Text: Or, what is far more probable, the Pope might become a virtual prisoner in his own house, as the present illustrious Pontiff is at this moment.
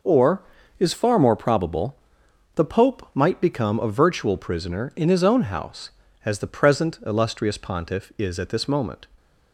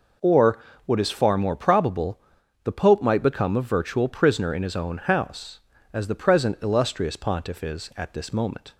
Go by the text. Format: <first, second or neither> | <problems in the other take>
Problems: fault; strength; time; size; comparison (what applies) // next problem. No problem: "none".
second | skips "what"; at 0.6 s